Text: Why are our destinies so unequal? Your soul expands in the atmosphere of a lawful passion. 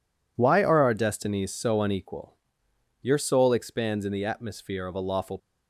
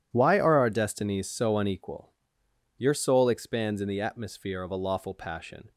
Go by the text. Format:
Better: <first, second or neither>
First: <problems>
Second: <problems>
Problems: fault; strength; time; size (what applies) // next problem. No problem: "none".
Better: second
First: stops before "passion"; at 5.3 s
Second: none